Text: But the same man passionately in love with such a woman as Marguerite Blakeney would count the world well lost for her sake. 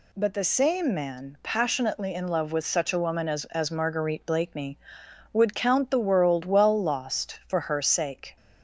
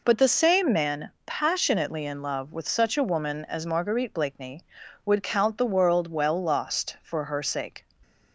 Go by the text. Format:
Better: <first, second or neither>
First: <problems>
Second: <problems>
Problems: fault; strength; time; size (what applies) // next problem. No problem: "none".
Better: second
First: says "as" twice; at 3.4 s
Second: none